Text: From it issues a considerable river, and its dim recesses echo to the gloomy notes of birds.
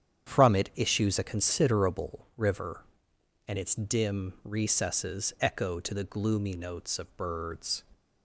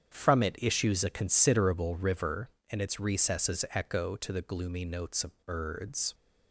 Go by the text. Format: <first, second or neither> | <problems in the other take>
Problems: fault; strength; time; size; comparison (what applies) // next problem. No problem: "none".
first | starts louder than the rest; strong; until 1.1 s; 8 dB; strong in the first // skips "dim"; at 3.0 s